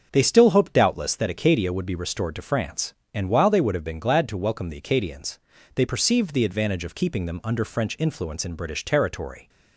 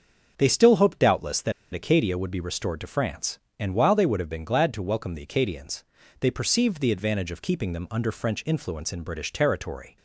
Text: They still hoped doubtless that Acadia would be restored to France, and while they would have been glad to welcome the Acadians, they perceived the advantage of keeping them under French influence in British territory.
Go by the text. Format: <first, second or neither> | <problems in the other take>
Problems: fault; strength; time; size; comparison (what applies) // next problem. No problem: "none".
first | starts louder than the rest; until 1.3 s; 7 dB; also in the first // pauses between "that" and "Acadia"; slight; at 1.5 s; 0.21 s long